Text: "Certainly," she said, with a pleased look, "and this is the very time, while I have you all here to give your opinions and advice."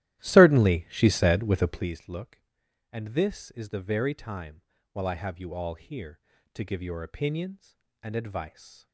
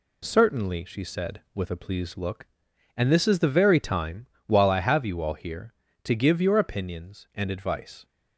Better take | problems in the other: second | starts louder than the rest; strong; until 1.9 s; 14 dB

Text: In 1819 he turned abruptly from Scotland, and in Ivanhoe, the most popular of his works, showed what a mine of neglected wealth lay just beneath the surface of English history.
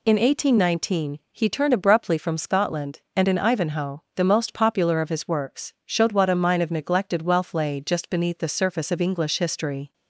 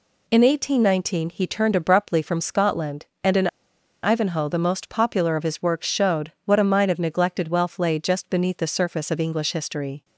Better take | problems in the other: first | pauses between "in" and "Ivanhoe"; noticeable; at 3.4 s; 0.56 s long

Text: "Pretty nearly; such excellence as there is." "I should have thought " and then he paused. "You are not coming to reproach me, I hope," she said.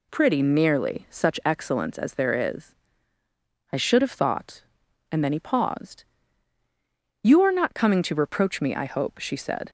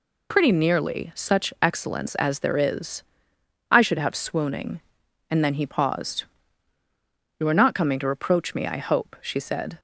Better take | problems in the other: first | says "swooning" for "thought"; at 4.1 s

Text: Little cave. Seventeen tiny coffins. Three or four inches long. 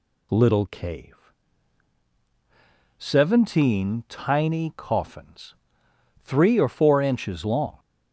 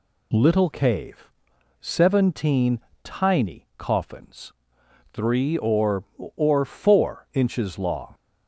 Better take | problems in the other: first | pauses between "Seventeen" and "tiny"; slight; at 2.7 s; 0.24 s long // says "or" twice; at 6.3 s

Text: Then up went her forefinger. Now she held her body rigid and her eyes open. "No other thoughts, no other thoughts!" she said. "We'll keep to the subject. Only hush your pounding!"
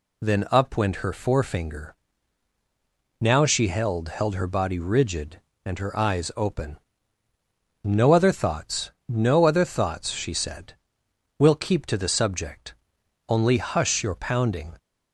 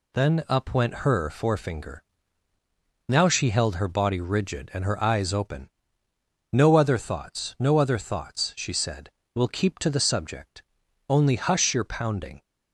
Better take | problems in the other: second | says "held" twice; at 4.0 s

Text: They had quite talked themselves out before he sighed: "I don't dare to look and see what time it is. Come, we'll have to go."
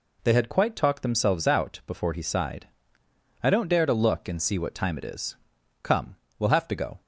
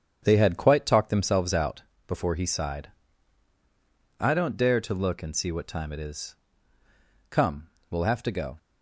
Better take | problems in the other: first | starts louder than the rest; strong; until 1.2 s; 8.5 dB // pauses between "out" and "before"; slight; at 1.8 s; 0.26 s long

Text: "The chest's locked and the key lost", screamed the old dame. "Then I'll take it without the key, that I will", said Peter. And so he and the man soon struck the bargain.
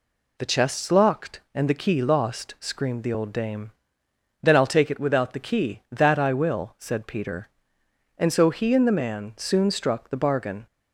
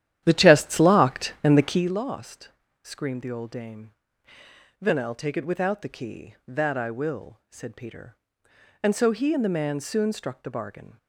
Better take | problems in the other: first | starts louder than the rest; strong; until 1.8 s; 11.5 dB

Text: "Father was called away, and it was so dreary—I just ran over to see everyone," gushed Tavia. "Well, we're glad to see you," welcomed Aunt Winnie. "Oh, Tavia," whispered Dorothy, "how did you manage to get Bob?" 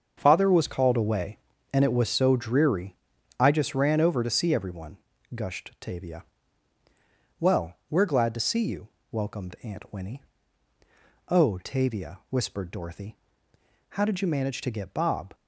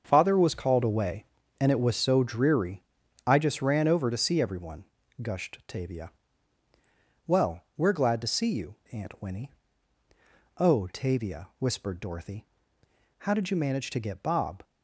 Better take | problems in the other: first | starts louder than the rest; until 1.0 s; 6.5 dB; also in the first // skips "welcomed"; at 8.8 s

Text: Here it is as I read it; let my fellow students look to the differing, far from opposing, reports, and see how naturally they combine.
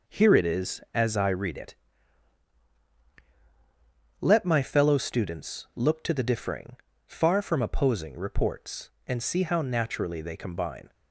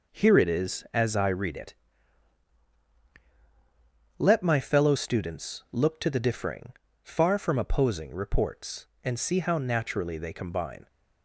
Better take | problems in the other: neither | none

